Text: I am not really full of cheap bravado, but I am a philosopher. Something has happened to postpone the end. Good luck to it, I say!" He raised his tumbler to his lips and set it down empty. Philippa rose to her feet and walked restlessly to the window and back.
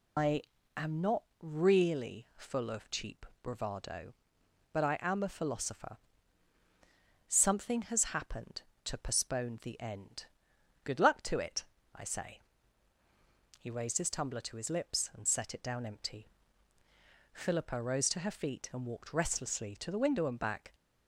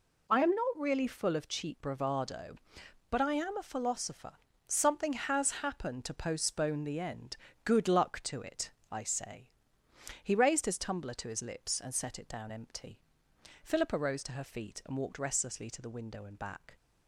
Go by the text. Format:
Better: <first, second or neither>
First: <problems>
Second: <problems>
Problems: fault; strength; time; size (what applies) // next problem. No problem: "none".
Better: second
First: loses the start of "I"; at 0.1 s; 155 ms // pauses between "I" and "am"; slight; at 0.4 s; 0.36 s long // pauses between "not" and "really"; slight; at 1.2 s; 0.18 s long // pauses between "cheap" and "bravado"; slight; at 3.2 s; 0.18 s long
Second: none